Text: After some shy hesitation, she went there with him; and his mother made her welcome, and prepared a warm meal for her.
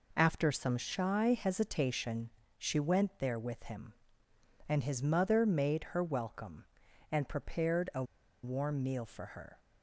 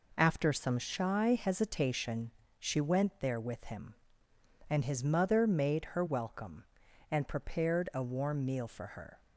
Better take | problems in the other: second | pauses between "a" and "warm"; at 8.0 s; 0.39 s long

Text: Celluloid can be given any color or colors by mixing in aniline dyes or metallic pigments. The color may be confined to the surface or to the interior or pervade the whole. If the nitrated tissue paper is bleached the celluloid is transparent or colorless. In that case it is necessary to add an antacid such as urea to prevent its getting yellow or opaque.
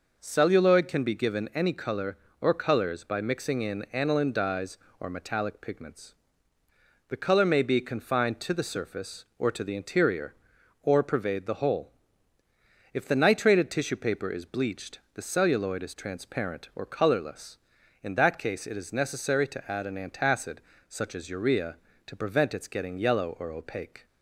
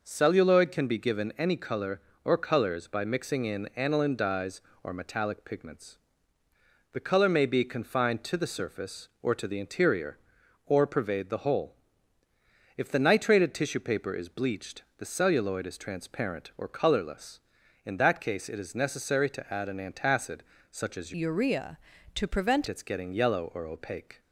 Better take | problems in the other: first | pauses between "bleached" and "the"; slight; at 14.8 s; 0.16 s long; slight in the first // pauses between "antacid" and "such"; slight; at 20.3 s; 0.30 s long; slight in the first // changes voice from "urea" to "prevent"; from 21.1 to 22.6 s; 1.5 s long

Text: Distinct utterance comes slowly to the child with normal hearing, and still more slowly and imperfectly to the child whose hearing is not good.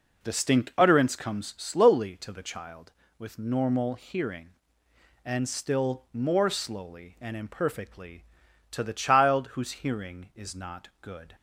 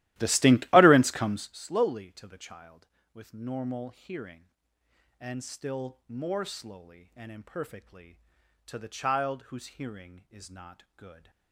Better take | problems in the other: first | starts louder than the rest; strong; until 1.6 s; 15.5 dB

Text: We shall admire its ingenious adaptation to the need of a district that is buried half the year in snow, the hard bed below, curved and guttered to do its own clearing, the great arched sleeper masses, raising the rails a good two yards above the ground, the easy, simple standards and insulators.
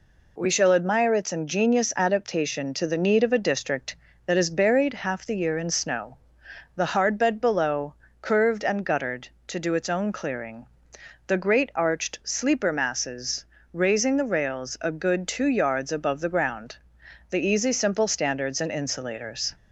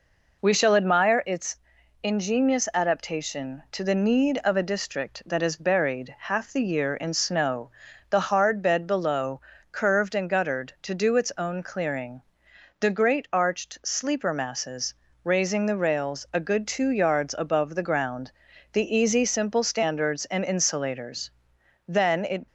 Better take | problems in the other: first | pauses between "its" and "ingenious"; at 1.5 s; 0.44 s long // goes on to say "Then it"; from 21.8 s on; 0.58 s long

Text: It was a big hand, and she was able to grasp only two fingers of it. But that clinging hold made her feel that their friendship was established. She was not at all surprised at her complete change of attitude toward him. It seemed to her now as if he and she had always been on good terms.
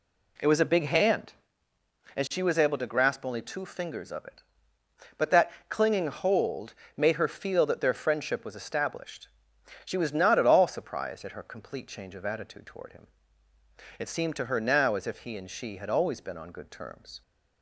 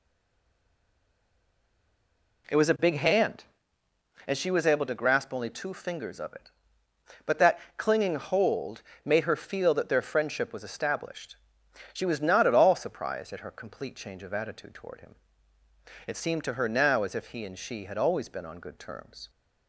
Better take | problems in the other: first | stays silent before the first word; until 2.4 s; 2.4 s long // pauses between "that" and "clinging"; slight; at 7.5 s; 0.16 s long; slight in the first // pauses between "hold" and "made"; slight; at 8.8 s; 0.22 s long; slight in the first

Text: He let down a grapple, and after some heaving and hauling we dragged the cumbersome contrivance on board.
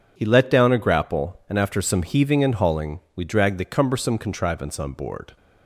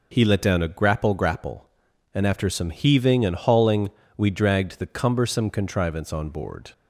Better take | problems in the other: first | says "grapple" twice; at 1.1 s // pauses between "hauling" and "we"; slight; at 3.8 s; 0.30 s long; slight in the first

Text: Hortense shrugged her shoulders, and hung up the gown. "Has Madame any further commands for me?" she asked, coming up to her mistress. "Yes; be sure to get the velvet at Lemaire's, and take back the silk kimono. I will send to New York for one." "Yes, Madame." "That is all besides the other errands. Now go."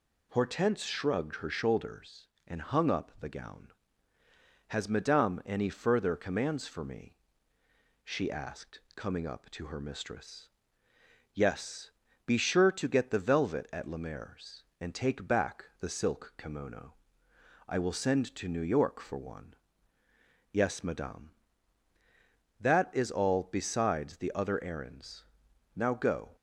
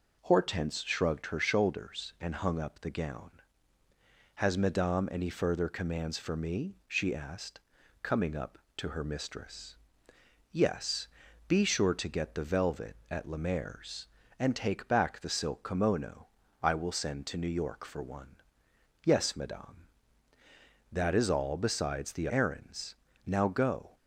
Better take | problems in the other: first | skips "other"; at 22.2 s

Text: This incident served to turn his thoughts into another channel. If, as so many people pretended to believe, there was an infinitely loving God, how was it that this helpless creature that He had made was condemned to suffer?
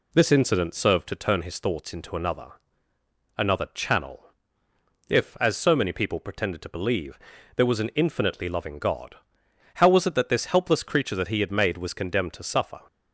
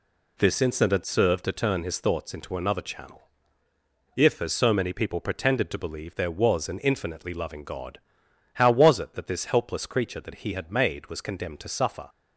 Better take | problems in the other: second | says "another" twice; at 3.3 s

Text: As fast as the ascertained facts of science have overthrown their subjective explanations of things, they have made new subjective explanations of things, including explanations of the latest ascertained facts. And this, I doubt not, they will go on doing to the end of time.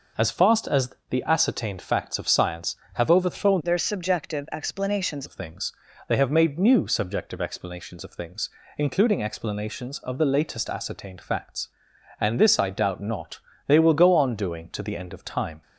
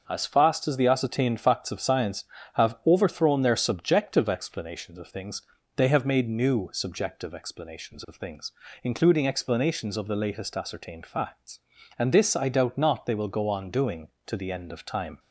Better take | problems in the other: second | changes voice from "their" to "explanations"; from 3.6 to 5.2 s; 1.6 s long

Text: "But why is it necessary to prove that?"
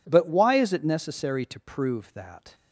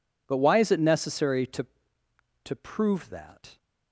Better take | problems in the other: first | says "to" twice; at 2.4 s

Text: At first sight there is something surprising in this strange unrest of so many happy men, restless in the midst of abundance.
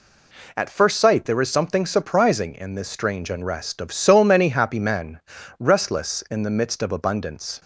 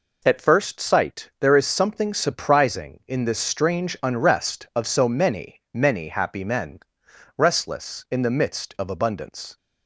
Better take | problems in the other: first | says "many" twice; at 5.7 s

